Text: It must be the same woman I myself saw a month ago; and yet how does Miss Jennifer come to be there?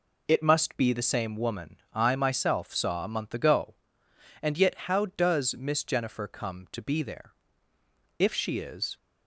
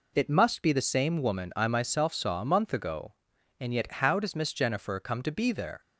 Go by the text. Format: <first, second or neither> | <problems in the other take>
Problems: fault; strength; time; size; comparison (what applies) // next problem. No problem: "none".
second | goes on to say "If she is"; noticeable; from 8.1 s on; 0.78 s long